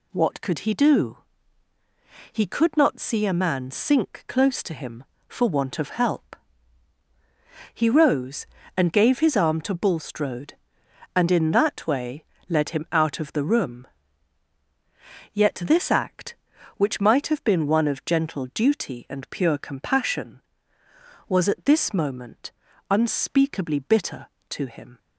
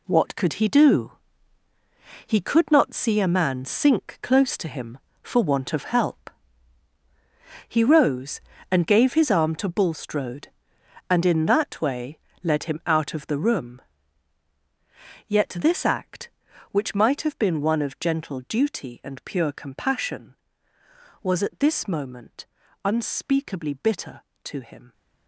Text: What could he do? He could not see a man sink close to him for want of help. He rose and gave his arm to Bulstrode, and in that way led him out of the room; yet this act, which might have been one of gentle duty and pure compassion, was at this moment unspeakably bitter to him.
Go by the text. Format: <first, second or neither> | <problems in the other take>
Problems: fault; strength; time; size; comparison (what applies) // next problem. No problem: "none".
first | gets quieter; strong; throughout; 10 dB // pauses between "way" and "led"; slight; at 12.1 s; 0.24 s long; slight in the first // pauses between "moment" and "unspeakably"; at 22.4 s; 0.40 s long; also in the first